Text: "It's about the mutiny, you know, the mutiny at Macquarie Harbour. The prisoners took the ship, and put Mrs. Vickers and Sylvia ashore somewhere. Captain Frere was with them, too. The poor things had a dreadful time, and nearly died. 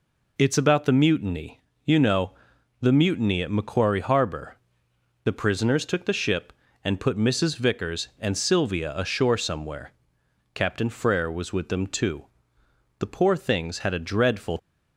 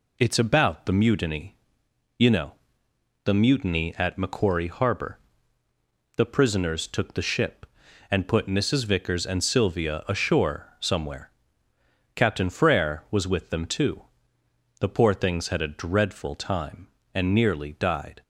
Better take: second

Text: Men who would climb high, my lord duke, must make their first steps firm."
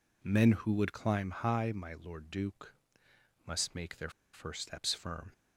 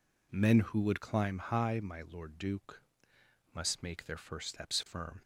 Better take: second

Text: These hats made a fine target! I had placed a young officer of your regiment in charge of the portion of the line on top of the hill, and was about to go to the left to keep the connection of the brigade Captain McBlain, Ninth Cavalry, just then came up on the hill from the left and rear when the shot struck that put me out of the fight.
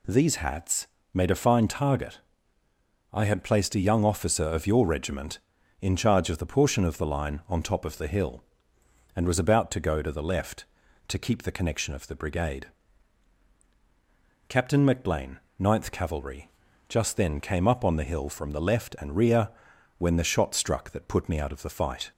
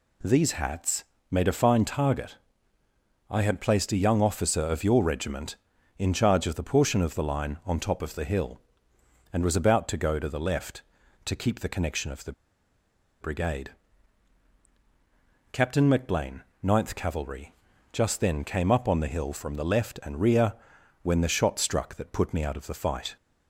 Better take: first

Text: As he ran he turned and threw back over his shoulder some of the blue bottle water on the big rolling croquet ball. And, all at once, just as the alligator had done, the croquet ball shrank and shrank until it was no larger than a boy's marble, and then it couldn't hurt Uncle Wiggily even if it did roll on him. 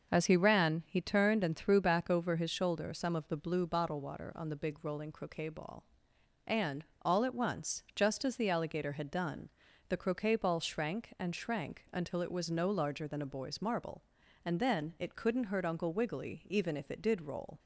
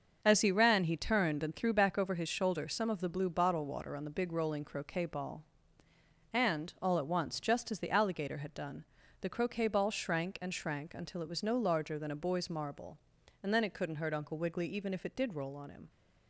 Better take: second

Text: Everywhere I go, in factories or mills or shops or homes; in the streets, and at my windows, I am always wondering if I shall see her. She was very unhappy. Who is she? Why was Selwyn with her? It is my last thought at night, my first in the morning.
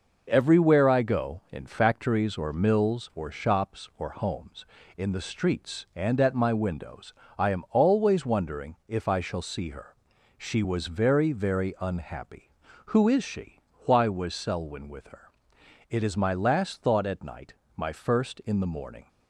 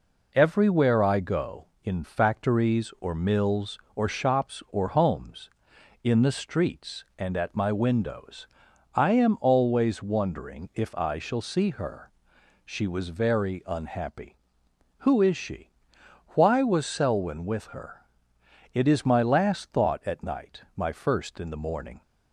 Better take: second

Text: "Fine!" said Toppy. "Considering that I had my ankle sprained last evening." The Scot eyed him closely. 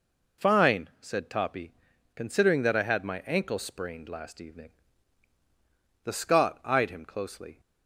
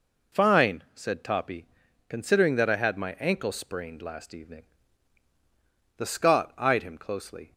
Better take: neither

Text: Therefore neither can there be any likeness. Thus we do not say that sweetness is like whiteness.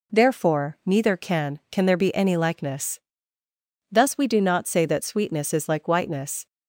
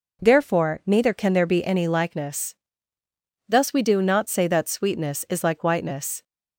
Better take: second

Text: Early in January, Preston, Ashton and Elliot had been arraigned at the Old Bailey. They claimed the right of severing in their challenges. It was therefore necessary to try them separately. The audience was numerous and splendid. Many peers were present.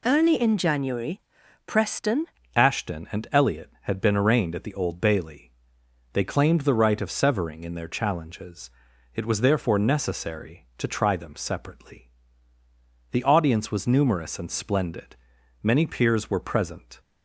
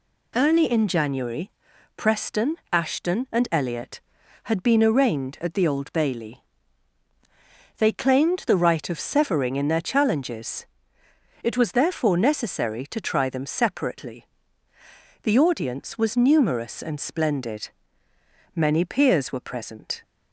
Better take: second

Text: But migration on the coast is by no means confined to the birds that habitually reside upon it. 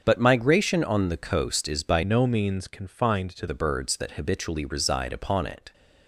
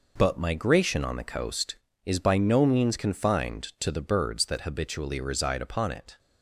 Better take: second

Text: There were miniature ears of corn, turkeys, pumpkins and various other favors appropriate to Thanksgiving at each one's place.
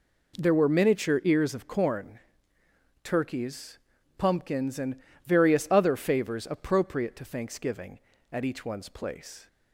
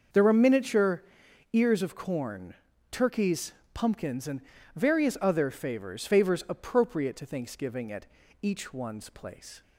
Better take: first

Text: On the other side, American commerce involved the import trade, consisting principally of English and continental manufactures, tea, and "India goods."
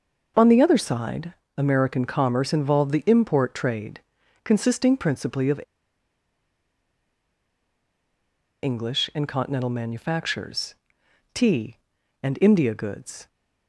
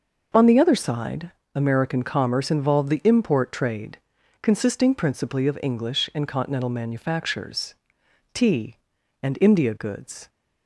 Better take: second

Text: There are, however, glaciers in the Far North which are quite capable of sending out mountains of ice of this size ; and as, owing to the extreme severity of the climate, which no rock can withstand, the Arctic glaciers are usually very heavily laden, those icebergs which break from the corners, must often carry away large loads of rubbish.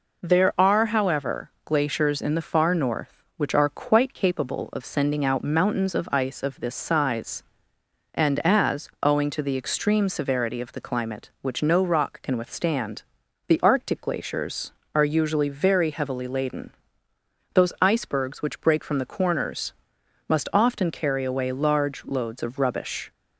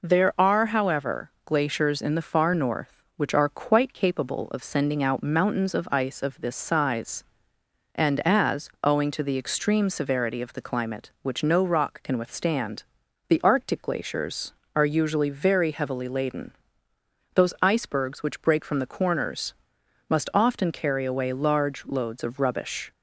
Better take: neither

